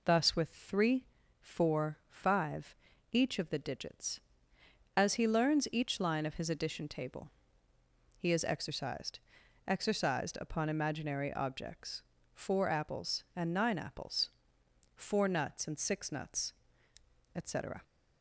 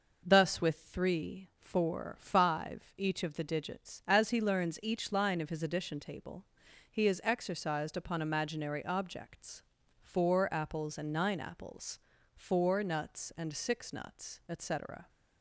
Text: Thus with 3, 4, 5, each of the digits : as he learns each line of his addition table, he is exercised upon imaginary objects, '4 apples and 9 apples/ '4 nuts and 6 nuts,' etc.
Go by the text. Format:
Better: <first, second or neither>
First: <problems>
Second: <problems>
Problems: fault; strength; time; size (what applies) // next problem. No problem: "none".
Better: second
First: says "exercised" twice; at 9.6 s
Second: none